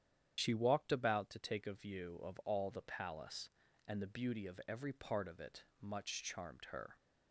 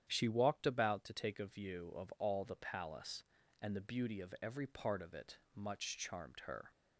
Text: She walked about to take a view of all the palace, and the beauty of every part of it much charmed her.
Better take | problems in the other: second | loses the start of "She"; at 0.3 s; 35 ms // starts louder than the rest; strong; until 1.3 s; 9.5 dB; strong in the second

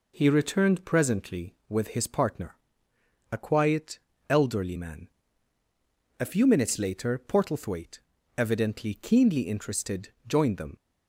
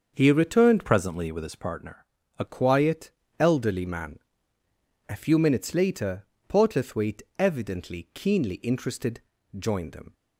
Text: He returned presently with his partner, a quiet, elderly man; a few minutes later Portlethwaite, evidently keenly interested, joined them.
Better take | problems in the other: first | starts louder than the rest; until 1.1 s; 6.5 dB // changes voice from "presently" to "a"; from 0.8 to 2.4 s; 1.6 s long // pauses between "later" and "Portlethwaite"; slight; at 6.2 s; 0.22 s long

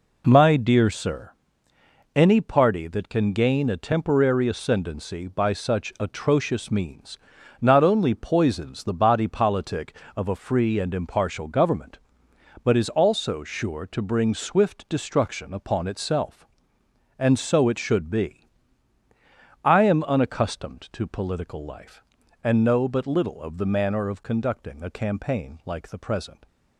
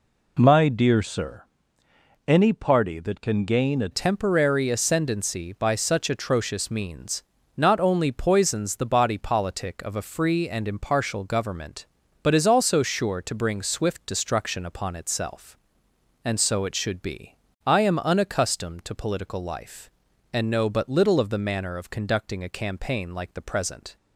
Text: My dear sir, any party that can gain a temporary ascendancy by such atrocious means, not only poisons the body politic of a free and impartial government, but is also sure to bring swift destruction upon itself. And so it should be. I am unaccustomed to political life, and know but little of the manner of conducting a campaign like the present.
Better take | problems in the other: first | changes voice at "temporary"; from 3.9 s on; 20.0 s long

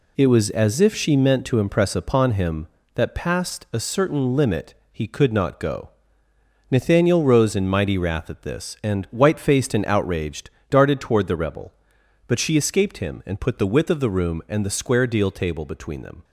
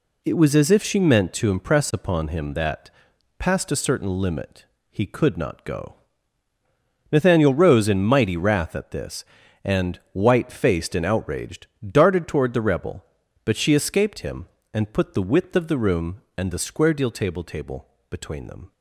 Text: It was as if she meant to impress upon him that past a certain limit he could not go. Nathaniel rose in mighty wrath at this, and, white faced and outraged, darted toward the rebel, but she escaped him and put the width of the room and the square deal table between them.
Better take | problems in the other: first | pauses between "that" and "past"; noticeable; at 2.8 s; 0.50 s long // pauses between "limit" and "he"; slight; at 4.6 s; 0.22 s long; slight in the first // says "table" twice; at 17.4 s

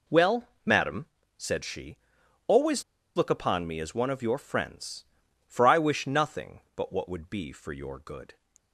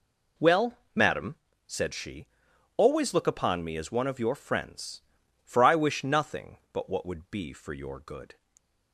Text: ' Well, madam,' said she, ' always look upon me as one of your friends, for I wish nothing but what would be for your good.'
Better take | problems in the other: second | pauses between "always" and "look"; slight; at 2.8 s; 0.34 s long

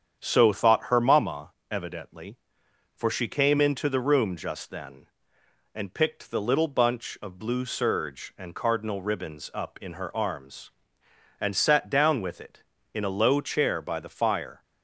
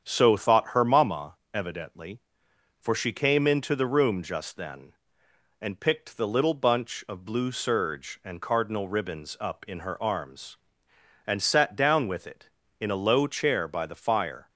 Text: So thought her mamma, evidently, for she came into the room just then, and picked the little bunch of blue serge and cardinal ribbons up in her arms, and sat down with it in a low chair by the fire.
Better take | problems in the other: neither | starts louder than the rest; strong; the same in both

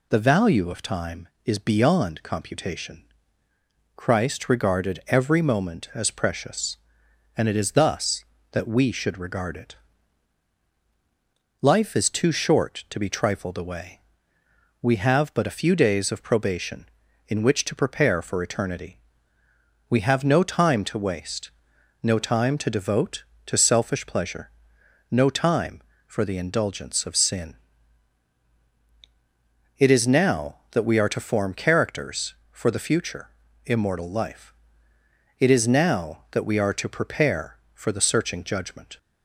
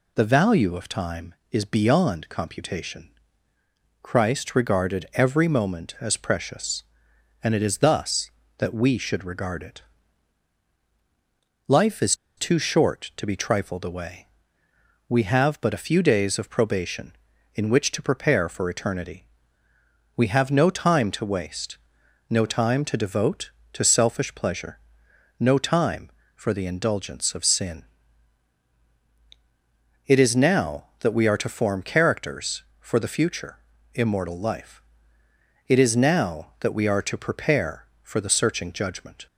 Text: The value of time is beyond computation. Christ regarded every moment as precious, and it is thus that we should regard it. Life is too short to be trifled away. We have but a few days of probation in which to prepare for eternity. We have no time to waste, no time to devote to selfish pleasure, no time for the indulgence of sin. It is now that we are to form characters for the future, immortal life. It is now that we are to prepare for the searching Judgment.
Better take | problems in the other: first | pauses between "is" and "too"; slight; at 12.1 s; 0.23 s long

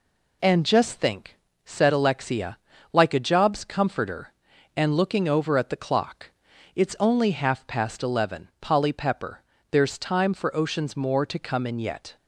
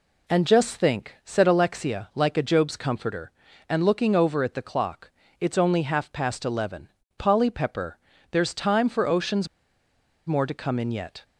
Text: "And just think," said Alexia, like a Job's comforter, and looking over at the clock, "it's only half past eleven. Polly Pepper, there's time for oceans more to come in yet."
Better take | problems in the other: first | pauses between "oceans" and "more"; noticeable; at 9.4 s; 0.80 s long

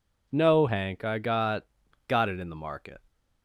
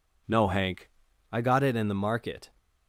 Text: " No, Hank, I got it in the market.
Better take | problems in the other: second | says "got" twice; at 2.0 s

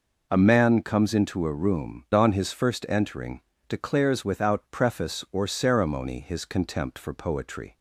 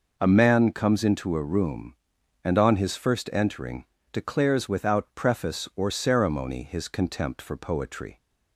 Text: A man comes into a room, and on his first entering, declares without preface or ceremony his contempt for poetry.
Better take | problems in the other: second | skips "and"; at 2.0 s

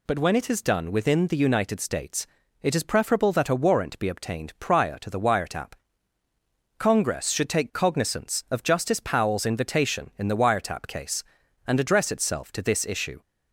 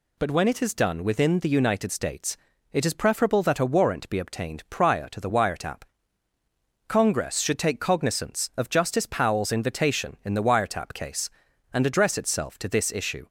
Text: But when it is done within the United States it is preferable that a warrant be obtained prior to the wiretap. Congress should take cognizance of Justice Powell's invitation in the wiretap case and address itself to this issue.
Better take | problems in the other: neither | pauses between "States" and "it"; slight; the same in both

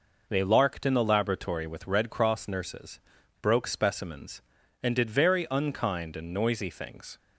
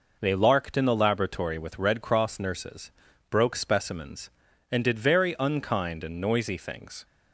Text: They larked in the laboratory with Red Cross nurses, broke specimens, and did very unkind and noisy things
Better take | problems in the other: neither | none

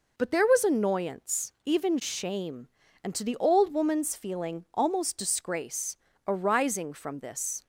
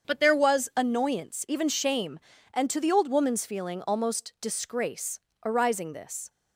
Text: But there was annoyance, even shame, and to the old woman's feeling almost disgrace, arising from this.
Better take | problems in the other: first | starts louder than the rest; strong; until 1.1 s; 7 dB // skips "from"; at 5.9 s

